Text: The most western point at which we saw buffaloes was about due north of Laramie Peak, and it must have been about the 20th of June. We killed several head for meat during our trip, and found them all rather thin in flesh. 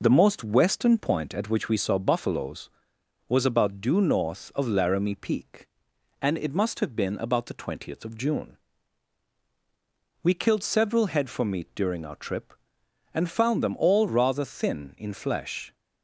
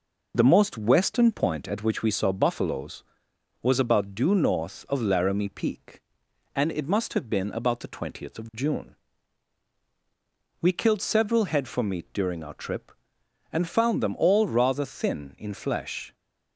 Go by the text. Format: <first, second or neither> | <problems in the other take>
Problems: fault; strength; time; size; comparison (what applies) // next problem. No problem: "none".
neither | none